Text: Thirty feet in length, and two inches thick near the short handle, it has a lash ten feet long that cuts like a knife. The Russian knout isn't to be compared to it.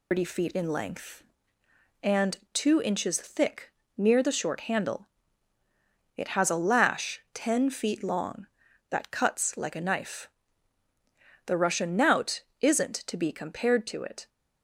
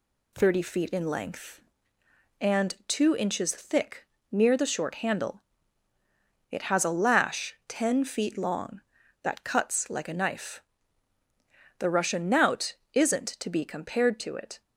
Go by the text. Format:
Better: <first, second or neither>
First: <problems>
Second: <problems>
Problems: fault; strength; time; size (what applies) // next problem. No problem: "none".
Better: second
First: loses the start of "Thirty"; at 0.1 s; 135 ms // pauses between "and" and "two"; slight; at 2.3 s; 0.15 s long // pauses between "thick" and "near"; slight; at 3.7 s; 0.24 s long // pauses between "knout" and "isn't"; slight; at 12.4 s; 0.18 s long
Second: pauses between "thick" and "near"; slight; at 4.0 s; 0.24 s long // pauses between "knout" and "isn't"; slight; at 12.7 s; 0.18 s long